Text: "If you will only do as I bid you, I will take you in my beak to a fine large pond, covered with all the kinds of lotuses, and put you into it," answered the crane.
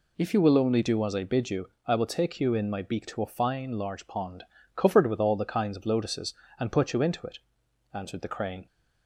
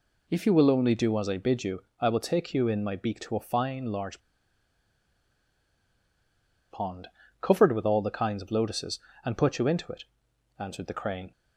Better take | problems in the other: first | pauses between "large" and "pond"; strong; at 4.1 s; 2.5 s long

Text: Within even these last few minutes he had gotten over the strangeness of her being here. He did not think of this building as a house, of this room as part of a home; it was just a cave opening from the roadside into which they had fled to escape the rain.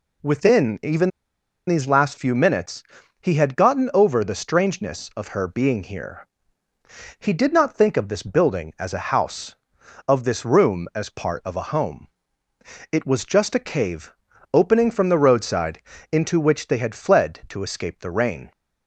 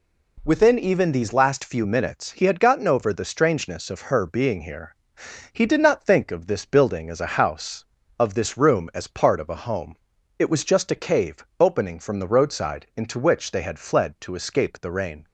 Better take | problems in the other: second | pauses between "even" and "these"; noticeable; at 1.1 s; 0.58 s long // pauses between "minutes" and "he"; slight; at 2.8 s; 0.36 s long // pauses between "cave" and "opening"; at 14.1 s; 0.40 s long // pauses between "roadside" and "into"; slight; at 15.8 s; 0.30 s long

